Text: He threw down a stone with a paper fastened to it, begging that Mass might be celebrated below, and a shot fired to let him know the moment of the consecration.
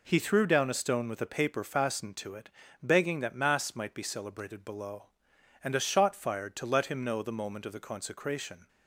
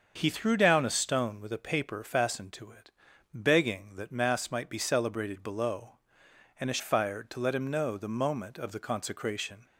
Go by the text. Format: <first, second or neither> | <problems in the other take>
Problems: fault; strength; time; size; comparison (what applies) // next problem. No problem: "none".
first | starts louder than the rest; until 1.1 s; 6.5 dB // skips "shot"; at 6.7 s